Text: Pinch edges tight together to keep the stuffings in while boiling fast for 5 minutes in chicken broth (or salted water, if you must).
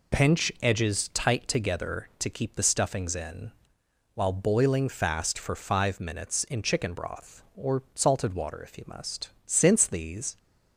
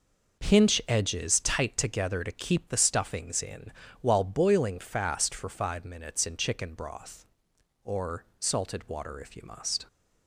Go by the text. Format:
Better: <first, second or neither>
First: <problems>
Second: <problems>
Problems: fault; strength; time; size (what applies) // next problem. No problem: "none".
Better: second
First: pauses between "in" and "while"; noticeable; at 3.4 s; 0.64 s long // goes on to say "Since these"; noticeable; from 9.4 s on; 0.90 s long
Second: pauses between "in" and "while"; slight; at 3.7 s; 0.28 s long